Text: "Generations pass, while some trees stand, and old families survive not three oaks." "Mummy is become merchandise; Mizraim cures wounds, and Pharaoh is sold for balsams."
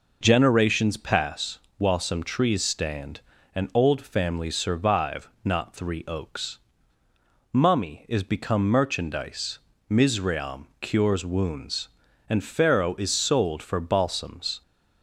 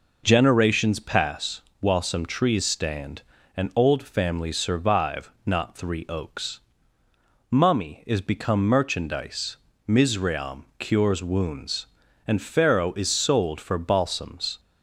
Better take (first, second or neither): neither